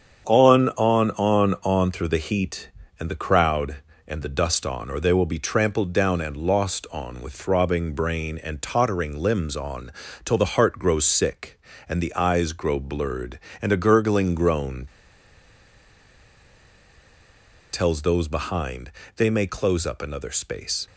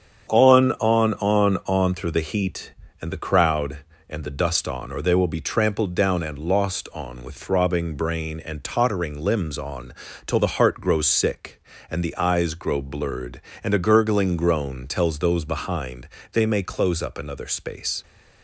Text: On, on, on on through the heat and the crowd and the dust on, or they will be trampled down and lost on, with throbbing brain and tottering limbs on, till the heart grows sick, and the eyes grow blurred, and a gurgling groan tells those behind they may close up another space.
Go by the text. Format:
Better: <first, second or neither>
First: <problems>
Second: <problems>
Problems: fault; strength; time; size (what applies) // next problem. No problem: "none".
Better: second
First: starts louder than the rest; strong; until 1.2 s; 7.5 dB // pauses between "groan" and "tells"; strong; at 14.8 s; 2.8 s long // pauses between "behind" and "they"; slight; at 18.9 s; 0.24 s long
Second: starts louder than the rest; strong; until 1.3 s; 7.5 dB // pauses between "behind" and "they"; slight; at 16.0 s; 0.23 s long